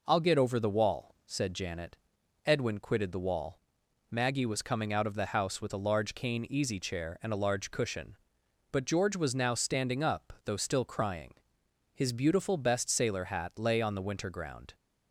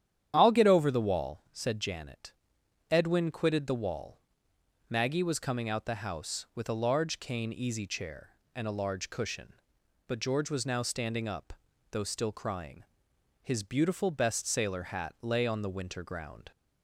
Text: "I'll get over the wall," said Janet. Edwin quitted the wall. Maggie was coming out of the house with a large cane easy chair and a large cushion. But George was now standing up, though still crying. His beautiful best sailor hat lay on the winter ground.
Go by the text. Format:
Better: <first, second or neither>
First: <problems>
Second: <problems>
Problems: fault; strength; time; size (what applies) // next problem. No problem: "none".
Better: first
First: none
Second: starts louder than the rest; strong; until 1.3 s; 10 dB // skips "of"; at 5.8 s